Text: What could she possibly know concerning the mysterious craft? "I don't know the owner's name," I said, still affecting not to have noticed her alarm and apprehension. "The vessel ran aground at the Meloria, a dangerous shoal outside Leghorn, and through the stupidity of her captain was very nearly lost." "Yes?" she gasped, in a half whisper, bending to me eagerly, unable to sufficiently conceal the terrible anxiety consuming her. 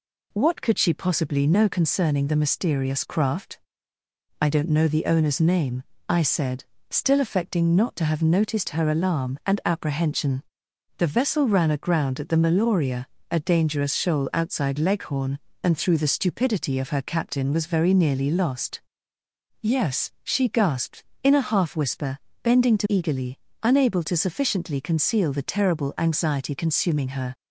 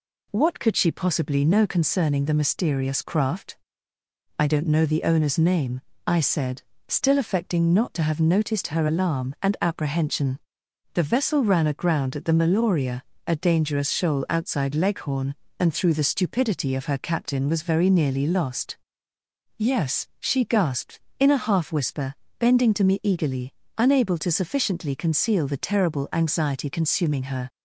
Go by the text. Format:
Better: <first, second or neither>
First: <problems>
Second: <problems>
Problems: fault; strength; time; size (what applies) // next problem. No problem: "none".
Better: second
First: skips "me"; at 22.8 s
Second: none